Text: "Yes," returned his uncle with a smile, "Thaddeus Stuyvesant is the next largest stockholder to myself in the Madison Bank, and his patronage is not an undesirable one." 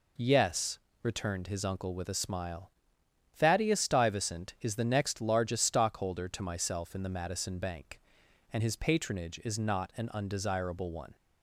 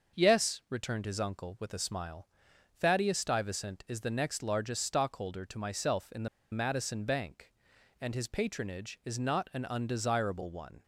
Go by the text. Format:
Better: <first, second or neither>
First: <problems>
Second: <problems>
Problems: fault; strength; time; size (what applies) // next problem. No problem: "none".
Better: first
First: none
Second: starts louder than the rest; until 1.2 s; 6 dB // pauses between "the" and "Madison"; slight; at 6.2 s; 0.24 s long